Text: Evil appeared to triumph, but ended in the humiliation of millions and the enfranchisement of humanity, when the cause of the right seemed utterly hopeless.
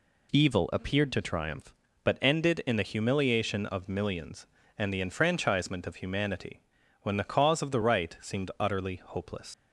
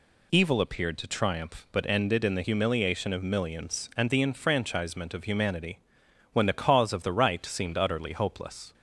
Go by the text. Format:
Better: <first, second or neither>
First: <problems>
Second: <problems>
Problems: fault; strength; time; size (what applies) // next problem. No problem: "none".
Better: second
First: leaves "hopeless" unfinished; at 9.5 s; 110 ms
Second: none